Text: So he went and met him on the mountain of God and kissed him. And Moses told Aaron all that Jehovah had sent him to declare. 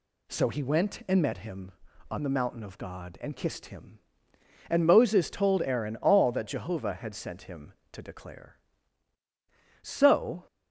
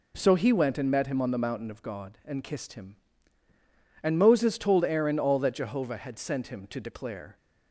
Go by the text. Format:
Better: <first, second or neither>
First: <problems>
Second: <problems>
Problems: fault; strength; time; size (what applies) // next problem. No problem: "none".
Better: second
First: goes on to say "So"; noticeable; from 9.8 s on; 0.64 s long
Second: none